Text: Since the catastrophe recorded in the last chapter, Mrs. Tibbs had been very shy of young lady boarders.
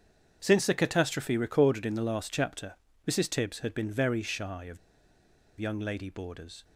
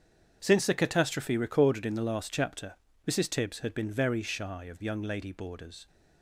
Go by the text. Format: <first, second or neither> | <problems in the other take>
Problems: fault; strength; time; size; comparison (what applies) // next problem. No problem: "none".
second | starts louder than the rest; strong; until 1.4 s; 7.5 dB; strong in the second // pauses between "of" and "young"; noticeable; at 4.7 s; 0.82 s long